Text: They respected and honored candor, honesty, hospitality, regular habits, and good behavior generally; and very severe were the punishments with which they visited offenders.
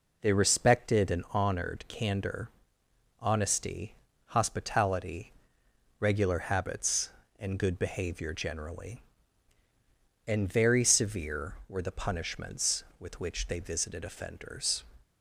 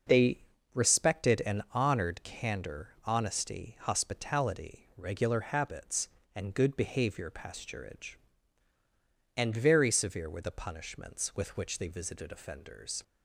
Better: first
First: none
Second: pauses between "They" and "respected"; slight; at 0.3 s; 0.33 s long // says "pasturage" for "generally"; at 7.2 s

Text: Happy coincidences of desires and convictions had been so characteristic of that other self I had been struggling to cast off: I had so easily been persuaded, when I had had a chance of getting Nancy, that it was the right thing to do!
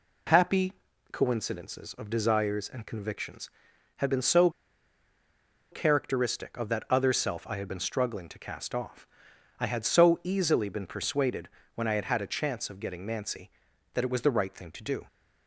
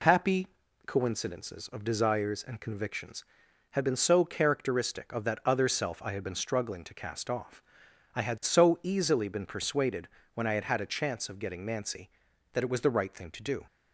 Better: second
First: pauses between "Happy" and "coincidences"; slight; at 0.7 s; 0.36 s long // pauses between "so" and "characteristic"; at 4.4 s; 1.2 s long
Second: pauses between "Happy" and "coincidences"; slight; at 0.4 s; 0.36 s long

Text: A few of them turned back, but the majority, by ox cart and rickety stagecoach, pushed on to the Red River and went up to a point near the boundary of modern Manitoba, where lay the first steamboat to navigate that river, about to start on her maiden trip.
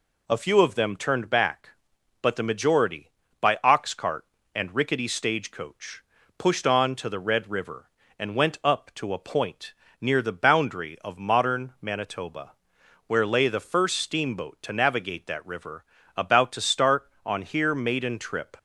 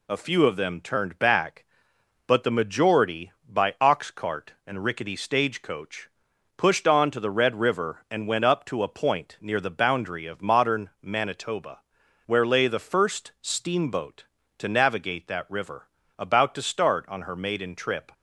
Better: second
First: pauses between "point" and "near"; slight; at 9.7 s; 0.28 s long // says "here" for "her"; at 17.4 s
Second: none

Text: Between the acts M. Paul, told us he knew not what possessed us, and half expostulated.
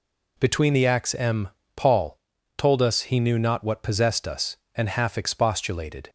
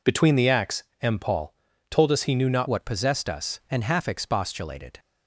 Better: first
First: none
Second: pauses between "acts" and "M"; slight; at 0.8 s; 0.20 s long // changes voice at "what"; from 2.6 s on; 2.3 s long

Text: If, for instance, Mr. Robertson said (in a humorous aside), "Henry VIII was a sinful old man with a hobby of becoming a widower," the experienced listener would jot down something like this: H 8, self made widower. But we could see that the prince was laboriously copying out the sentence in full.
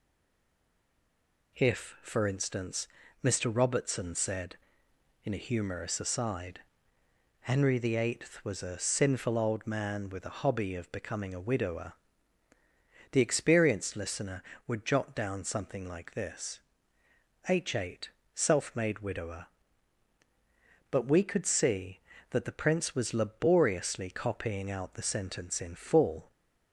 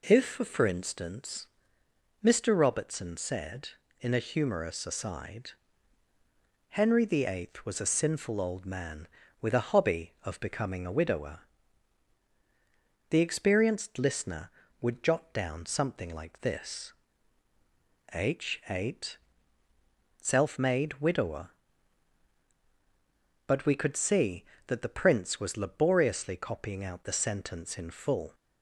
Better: second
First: stays silent before the first word; noticeable; until 1.5 s; 1.5 s long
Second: none

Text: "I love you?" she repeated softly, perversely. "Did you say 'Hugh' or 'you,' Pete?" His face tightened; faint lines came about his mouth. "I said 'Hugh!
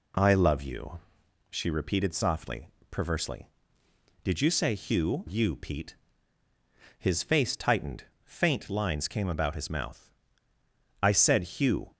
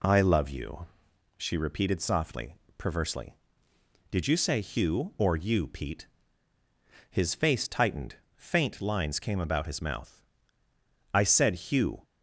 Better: second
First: skips "or"; at 5.2 s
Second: none

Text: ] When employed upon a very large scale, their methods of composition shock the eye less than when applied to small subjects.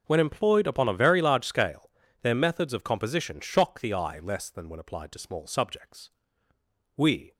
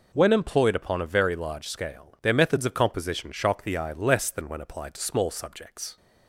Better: second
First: starts louder than the rest; noticeable; until 1.0 s; 6 dB // goes on to say "We"; slight; from 6.9 s on; 0.38 s long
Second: none

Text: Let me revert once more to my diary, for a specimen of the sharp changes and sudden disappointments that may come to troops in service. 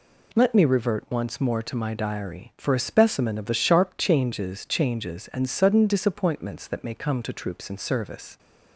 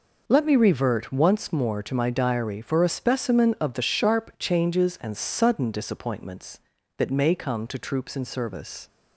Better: second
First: says "changes" twice; at 4.6 s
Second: none

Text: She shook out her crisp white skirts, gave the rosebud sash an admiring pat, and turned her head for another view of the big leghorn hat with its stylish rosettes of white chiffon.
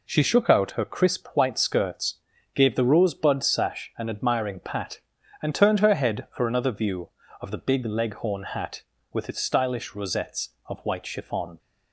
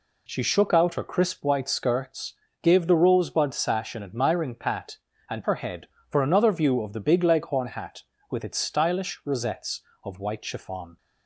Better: first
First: none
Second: skips "turned"; at 5.4 s

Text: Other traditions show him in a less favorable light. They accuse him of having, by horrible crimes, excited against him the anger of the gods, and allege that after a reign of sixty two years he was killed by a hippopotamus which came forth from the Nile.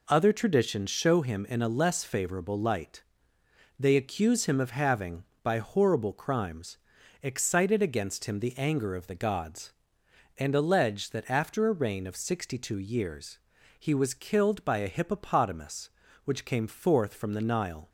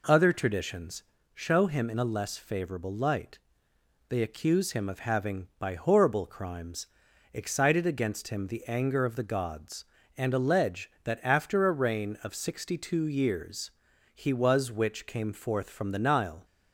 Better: first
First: pauses between "years" and "he"; at 13.3 s; 0.40 s long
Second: pauses between "traditions" and "show"; slight; at 1.0 s; 0.30 s long // pauses between "years" and "he"; at 13.7 s; 0.42 s long // skips "killed by a hippopotamus"; at 14.7 s

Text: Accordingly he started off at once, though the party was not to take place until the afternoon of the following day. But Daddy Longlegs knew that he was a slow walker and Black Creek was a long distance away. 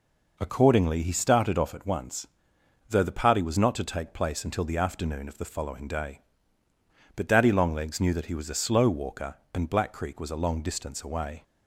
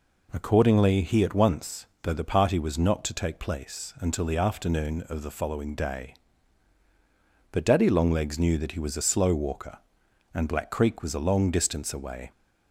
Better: first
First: none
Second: skips "started off"; at 1.2 s

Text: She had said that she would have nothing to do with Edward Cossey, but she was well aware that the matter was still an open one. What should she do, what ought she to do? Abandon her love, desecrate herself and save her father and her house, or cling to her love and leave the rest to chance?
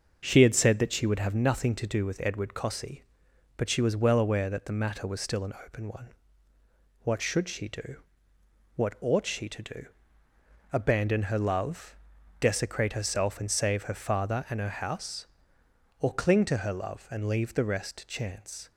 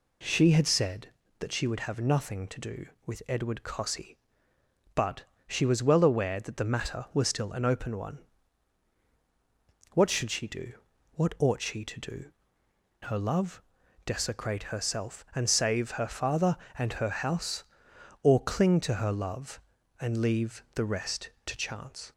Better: first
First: none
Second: pauses between "but" and "she"; slight; at 5.2 s; 0.24 s long // skips "Abandon"; at 12.6 s

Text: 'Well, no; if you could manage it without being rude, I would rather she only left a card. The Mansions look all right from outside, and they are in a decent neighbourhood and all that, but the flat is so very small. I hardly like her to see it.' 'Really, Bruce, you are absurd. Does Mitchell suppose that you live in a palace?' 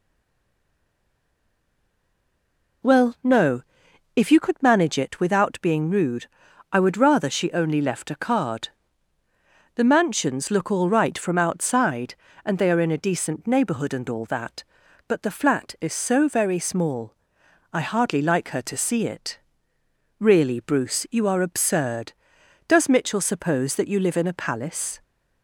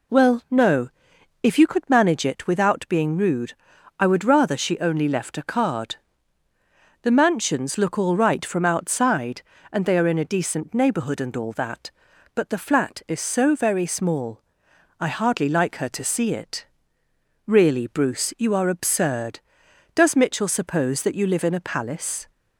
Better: second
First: stays silent before the first word; strong; until 2.8 s; 2.8 s long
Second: none

